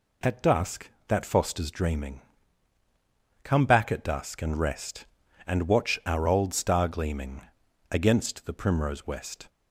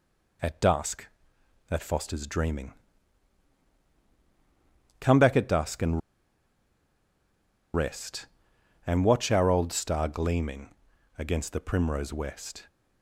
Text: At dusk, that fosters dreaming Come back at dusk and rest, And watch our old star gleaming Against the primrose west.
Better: first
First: pauses between "dreaming" and "Come"; at 2.2 s; 1.2 s long // pauses between "gleaming" and "Against"; noticeable; at 7.4 s; 0.50 s long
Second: pauses between "dreaming" and "Come"; strong; at 2.7 s; 2.3 s long // pauses between "and" and "rest"; strong; at 6.0 s; 1.7 s long // pauses between "gleaming" and "Against"; noticeable; at 10.6 s; 0.48 s long

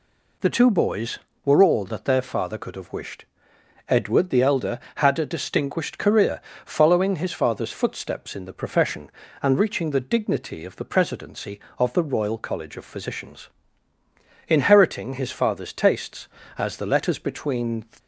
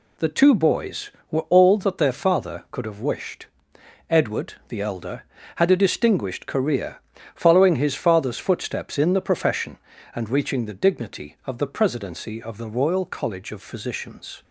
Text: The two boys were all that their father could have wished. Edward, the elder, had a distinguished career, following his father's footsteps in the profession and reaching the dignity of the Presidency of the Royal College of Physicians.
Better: second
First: goes on to say "Inheriting his father's tastes as the letters between"; strong; from 14.4 s on; 3.3 s long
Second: none

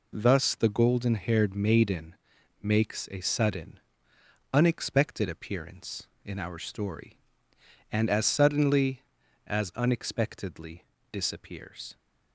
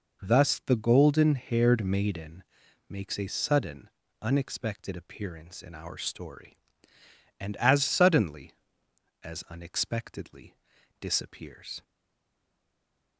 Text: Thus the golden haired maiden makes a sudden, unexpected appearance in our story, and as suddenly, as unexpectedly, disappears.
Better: first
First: pauses between "maiden" and "makes"; noticeable; at 2.1 s; 0.48 s long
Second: pauses between "maiden" and "makes"; noticeable; at 2.4 s; 0.46 s long // stays silent after the last word; noticeable; from 11.8 s on; 1.3 s long

